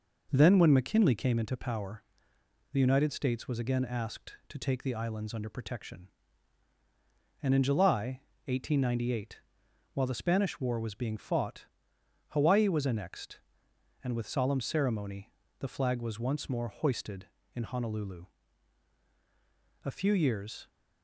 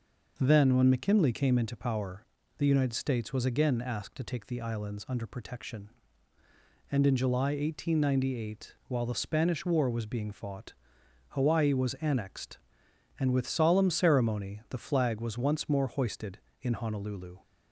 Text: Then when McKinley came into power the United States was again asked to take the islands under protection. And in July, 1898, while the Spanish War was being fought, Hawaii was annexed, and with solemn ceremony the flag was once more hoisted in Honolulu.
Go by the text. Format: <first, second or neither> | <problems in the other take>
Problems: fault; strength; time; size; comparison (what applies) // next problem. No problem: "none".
second | pauses between "power" and "the"; noticeable; at 2.0 s; 0.68 s long; slight in the second // pauses between "ceremony" and "the"; slight; at 15.3 s; 0.26 s long // goes on to say "A few years"; noticeable; from 19.8 s on; 0.84 s long